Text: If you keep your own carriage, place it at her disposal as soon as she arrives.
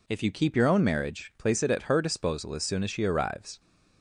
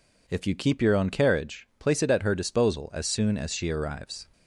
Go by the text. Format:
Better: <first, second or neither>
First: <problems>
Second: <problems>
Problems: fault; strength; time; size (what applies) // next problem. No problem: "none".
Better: second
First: says "marriage" for "carriage"; at 0.8 s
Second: none